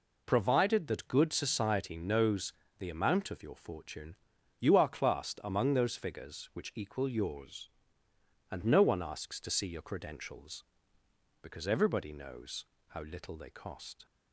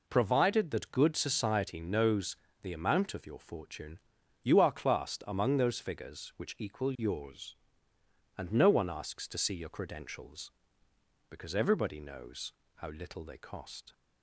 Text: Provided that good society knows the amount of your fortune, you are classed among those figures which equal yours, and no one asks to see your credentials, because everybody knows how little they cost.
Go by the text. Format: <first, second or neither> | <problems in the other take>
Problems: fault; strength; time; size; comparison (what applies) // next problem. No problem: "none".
neither | pauses between "knows" and "the"; slight; the same in both // pauses between "knows" and "how"; slight; the same in both